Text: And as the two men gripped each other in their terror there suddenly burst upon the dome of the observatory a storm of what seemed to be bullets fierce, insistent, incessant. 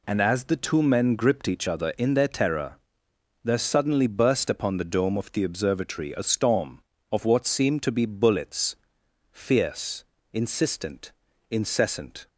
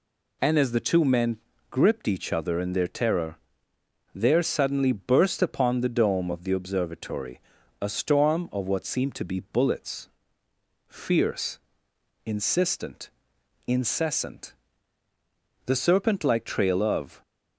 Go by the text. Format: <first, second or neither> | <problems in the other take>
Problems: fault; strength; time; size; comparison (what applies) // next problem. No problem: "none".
first | pauses between "men" and "gripped"; slight; at 1.3 s; 0.32 s long // pauses between "terror" and "there"; noticeable; at 3.3 s; 0.78 s long; noticeable in the first // pauses between "observatory" and "a"; at 7.3 s; 0.42 s long // pauses between "bullets" and "fierce"; noticeable; at 10.0 s; 0.80 s long; noticeable in the first // goes on to say "The serpent like trail of"; from 15.6 s on; 1.5 s long